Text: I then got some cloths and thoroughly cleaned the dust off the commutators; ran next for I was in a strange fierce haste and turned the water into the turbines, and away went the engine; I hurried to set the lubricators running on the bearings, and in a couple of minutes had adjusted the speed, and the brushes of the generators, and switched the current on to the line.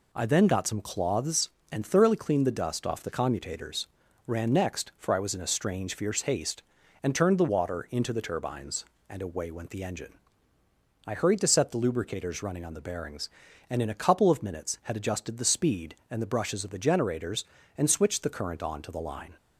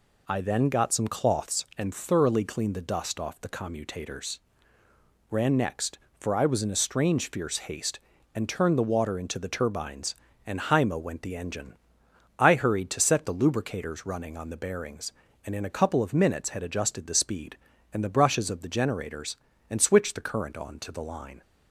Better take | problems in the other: first | says "haima" for "away"; at 10.5 s

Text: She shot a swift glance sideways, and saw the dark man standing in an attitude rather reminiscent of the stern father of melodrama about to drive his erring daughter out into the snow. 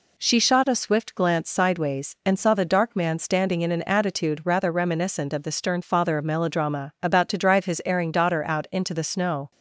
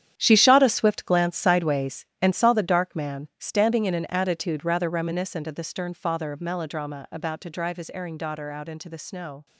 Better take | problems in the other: first | gets quieter; strong; throughout; 11.5 dB

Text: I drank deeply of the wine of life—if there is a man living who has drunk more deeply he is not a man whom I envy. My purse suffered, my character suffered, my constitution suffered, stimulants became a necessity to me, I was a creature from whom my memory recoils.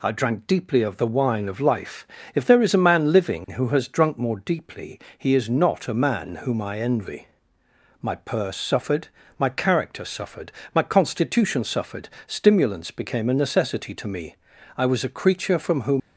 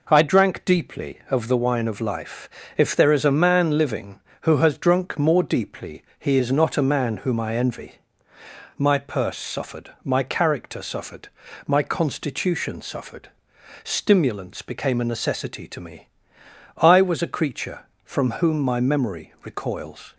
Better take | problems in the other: second | pauses between "deeply" and "he"; slight; at 4.9 s; 0.18 s long; slight in the second // stops before "my memory recoils"; at 16.0 s

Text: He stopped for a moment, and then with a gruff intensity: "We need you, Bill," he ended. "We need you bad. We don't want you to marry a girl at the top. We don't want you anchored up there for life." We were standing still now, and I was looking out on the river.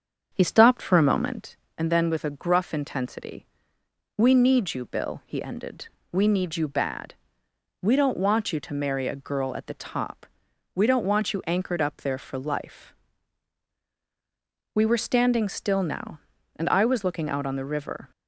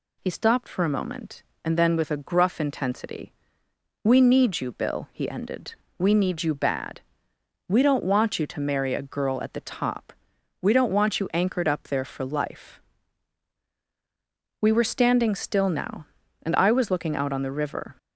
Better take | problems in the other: second | starts louder than the rest; strong; until 1.5 s; 7.5 dB

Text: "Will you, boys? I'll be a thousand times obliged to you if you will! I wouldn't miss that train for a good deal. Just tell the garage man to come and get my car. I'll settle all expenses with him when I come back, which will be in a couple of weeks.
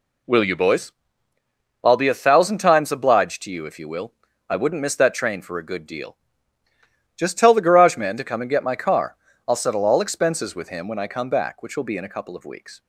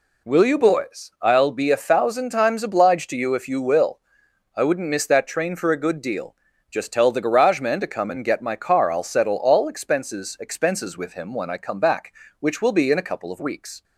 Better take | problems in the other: first | says "expenses" twice; at 10.3 s

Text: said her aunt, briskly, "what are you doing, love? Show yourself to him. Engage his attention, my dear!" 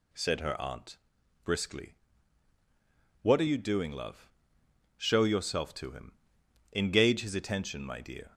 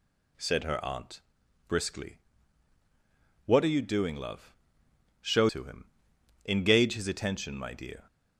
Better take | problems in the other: first | skips "yourself"; at 5.4 s

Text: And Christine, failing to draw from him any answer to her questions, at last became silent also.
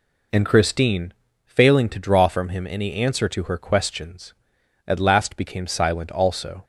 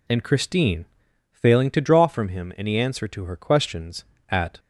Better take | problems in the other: first | stops before "last became silent also"; at 4.5 s

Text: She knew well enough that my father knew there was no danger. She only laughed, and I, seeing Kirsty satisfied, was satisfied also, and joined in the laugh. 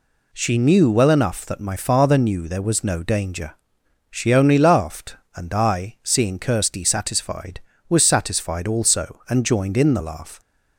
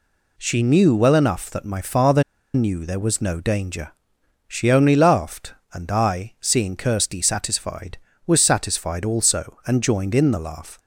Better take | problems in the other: first | pauses between "father" and "knew"; slight; at 2.2 s; 0.31 s long

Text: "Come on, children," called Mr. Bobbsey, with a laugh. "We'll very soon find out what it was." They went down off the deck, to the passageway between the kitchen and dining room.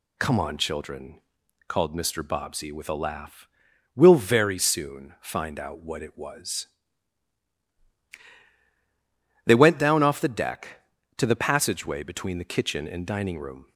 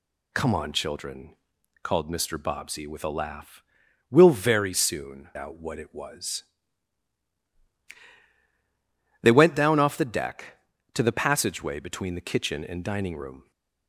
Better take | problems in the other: first | skips "find"; at 5.3 s

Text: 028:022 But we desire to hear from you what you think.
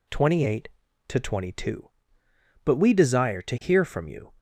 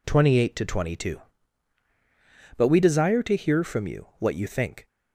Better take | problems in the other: second | stops before "what you think"; at 4.3 s

